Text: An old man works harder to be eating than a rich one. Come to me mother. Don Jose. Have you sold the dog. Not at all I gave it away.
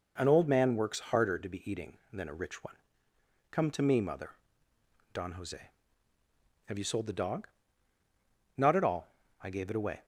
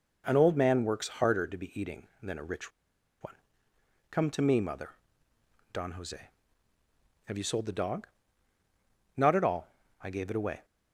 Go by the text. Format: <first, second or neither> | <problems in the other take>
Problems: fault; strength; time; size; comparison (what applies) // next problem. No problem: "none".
first | pauses between "rich" and "one"; noticeable; at 2.7 s; 0.51 s long // pauses between "all" and "I"; slight; at 9.6 s; 0.34 s long; slight in the first